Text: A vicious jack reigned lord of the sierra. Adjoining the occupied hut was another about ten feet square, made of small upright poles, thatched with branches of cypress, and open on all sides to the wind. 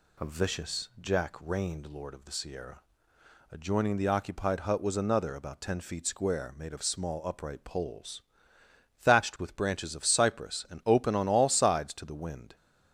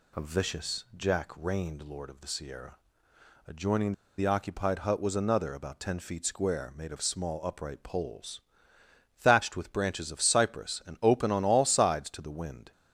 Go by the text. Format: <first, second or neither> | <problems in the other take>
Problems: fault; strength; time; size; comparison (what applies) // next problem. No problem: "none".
first | pauses between "Adjoining" and "the"; slight; at 3.9 s; 0.25 s long